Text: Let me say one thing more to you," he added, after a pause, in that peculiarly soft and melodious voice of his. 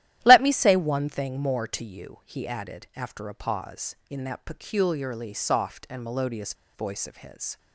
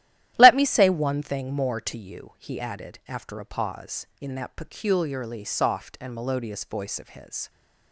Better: second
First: starts louder than the rest; strong; until 1.2 s; 13 dB // pauses between "melodious" and "voice"; slight; at 6.5 s; 0.21 s long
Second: starts louder than the rest; strong; until 1.3 s; 13 dB

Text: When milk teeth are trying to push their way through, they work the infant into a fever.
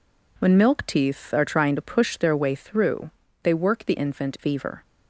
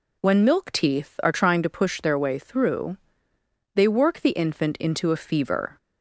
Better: second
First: skips "into a"; at 4.3 s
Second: none

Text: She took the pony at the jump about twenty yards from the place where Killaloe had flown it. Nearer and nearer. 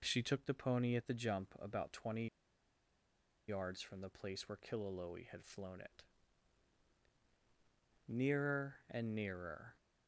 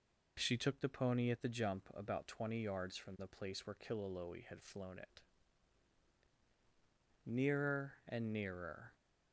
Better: second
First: pauses between "twenty" and "yards"; at 2.2 s; 1.2 s long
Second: none

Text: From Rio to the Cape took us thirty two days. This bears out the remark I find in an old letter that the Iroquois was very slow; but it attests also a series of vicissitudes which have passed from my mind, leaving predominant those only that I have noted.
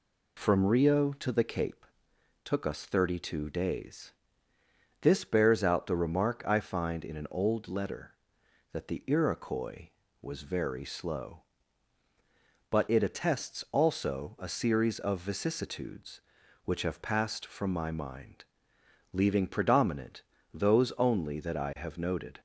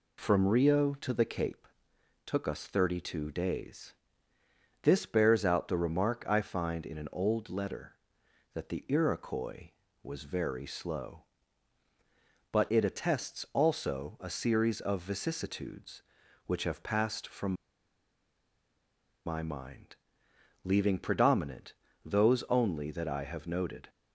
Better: first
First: pauses between "Cape" and "took"; noticeable; at 1.8 s; 0.60 s long // pauses between "predominant" and "those"; slight; at 20.2 s; 0.32 s long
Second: pauses between "Cape" and "took"; noticeable; at 1.6 s; 0.60 s long // pauses between "from" and "my"; strong; at 17.5 s; 1.7 s long // pauses between "predominant" and "those"; slight; at 21.7 s; 0.32 s long

